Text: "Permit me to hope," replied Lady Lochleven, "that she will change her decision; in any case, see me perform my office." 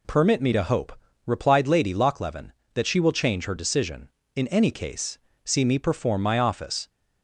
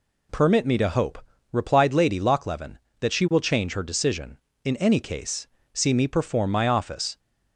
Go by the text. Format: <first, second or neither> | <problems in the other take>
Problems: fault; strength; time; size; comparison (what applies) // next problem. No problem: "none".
neither | none